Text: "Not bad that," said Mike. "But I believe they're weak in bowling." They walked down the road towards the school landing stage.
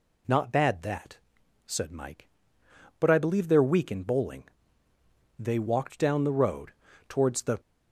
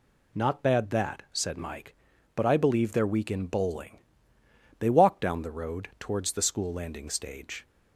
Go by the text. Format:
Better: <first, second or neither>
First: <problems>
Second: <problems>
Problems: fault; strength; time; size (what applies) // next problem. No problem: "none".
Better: second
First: pauses between "road" and "towards"; slight; at 6.7 s; 0.36 s long // stops before "school landing stage"; at 7.5 s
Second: none